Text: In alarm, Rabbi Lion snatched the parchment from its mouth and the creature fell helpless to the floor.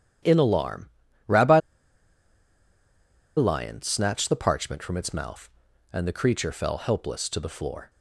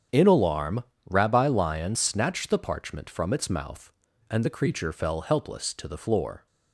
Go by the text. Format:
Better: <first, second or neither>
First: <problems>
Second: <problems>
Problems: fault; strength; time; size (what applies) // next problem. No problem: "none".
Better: second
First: starts louder than the rest; strong; until 3.4 s; 10.5 dB // pauses between "Rabbi" and "Lion"; strong; at 1.5 s; 1.7 s long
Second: starts louder than the rest; strong; until 1.3 s; 8.5 dB